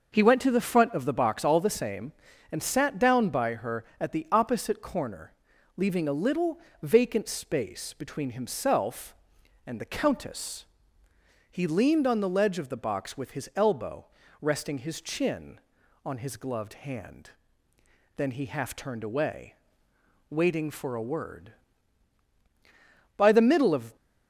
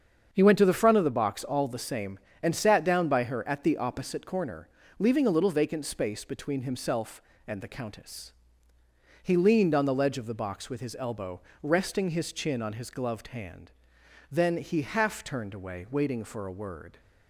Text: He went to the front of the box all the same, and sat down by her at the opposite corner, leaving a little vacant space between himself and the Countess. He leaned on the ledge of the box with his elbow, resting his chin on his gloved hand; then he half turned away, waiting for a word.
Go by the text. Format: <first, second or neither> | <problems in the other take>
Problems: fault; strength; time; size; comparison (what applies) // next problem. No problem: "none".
second | starts louder than the rest; noticeable; until 1.1 s; 6 dB; strong in the second // pauses between "little" and "vacant"; slight; at 6.5 s; 0.24 s long // goes on to say "By the middle of"; noticeable; from 23.1 s on; 0.78 s long